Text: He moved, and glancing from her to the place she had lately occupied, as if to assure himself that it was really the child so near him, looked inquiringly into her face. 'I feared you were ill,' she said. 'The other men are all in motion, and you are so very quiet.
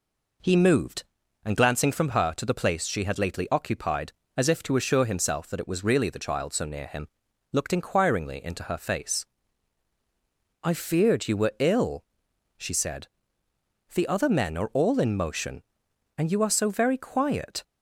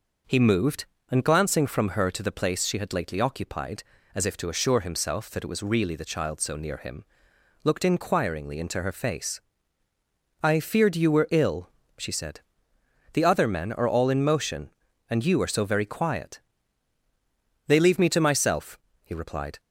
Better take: first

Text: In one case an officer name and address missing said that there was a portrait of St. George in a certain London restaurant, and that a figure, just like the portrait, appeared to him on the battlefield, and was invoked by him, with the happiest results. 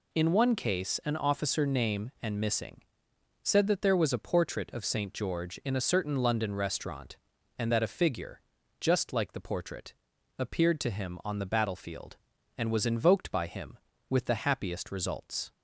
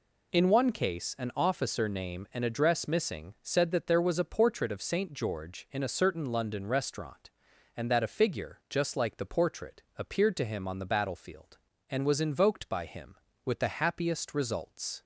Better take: second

